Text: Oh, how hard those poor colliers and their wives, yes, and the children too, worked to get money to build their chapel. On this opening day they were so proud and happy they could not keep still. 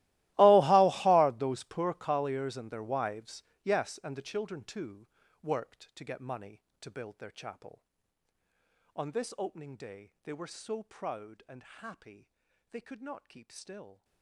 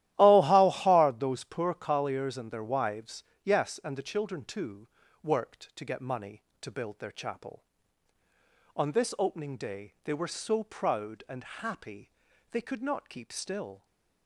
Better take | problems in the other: second | gets quieter; strong; throughout; 20.5 dB // starts louder than the rest; strong; until 1.3 s; 17.5 dB; strong in the second // pauses between "happy" and "they"; at 12.3 s; 0.42 s long; also in the second

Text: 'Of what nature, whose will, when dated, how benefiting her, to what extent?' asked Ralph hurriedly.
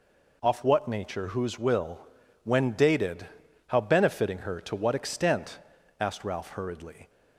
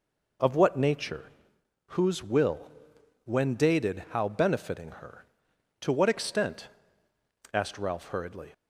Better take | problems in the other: second | says "Off" for "Of"; at 0.4 s

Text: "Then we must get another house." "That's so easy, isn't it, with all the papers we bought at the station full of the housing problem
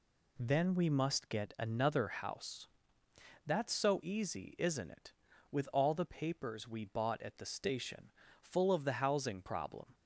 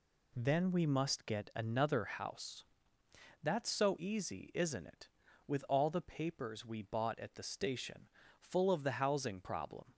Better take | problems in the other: neither | pauses between "station" and "full"; slight; the same in both

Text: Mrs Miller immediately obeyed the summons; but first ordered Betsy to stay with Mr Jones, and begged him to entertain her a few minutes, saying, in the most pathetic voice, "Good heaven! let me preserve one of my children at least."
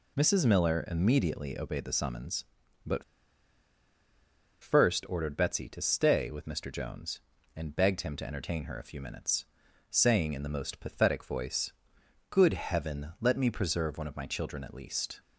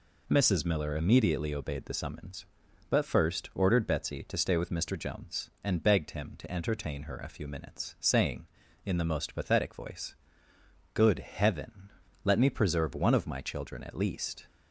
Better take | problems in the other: second | pauses between "but" and "first"; strong; at 3.0 s; 1.5 s long

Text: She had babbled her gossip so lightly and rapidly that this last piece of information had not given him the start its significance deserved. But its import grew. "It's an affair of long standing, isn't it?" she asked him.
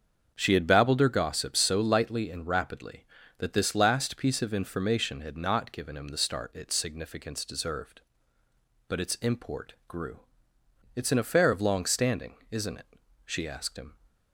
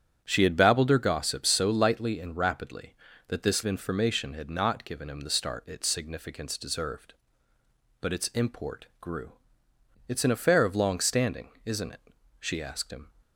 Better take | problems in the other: first | starts louder than the rest; strong; until 1.2 s; 8.5 dB; also in the first // skips "last piece of"; at 3.6 s

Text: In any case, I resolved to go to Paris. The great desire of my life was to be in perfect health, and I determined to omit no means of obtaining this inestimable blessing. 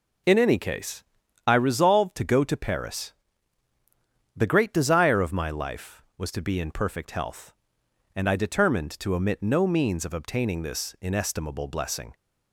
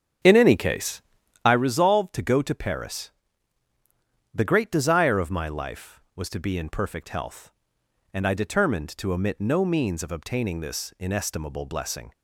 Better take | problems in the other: first | starts louder than the rest; strong; until 1.5 s; 8 dB

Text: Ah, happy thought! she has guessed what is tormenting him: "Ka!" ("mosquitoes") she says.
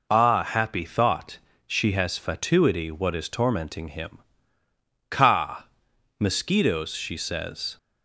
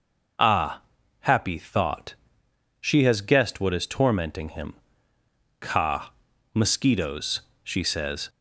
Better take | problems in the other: second | says "fatuity" for "guessed"; at 2.1 s

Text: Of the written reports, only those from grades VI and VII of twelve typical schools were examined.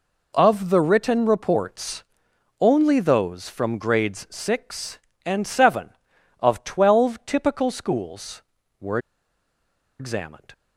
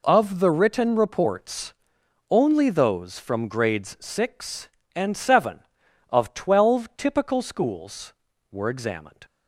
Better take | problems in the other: second | pauses between "were" and "examined"; at 8.9 s; 1.0 s long

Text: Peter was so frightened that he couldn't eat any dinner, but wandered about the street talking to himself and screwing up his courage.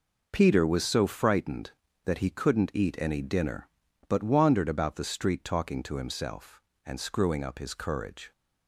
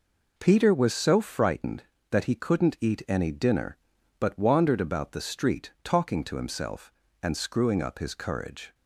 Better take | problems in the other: neither | none

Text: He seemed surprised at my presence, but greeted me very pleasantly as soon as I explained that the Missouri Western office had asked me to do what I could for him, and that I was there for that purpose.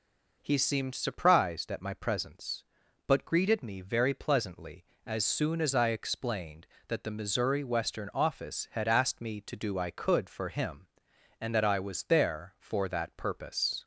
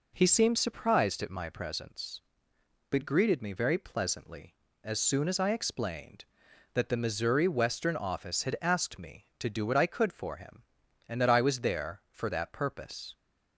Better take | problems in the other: second | skips "what"; at 9.7 s

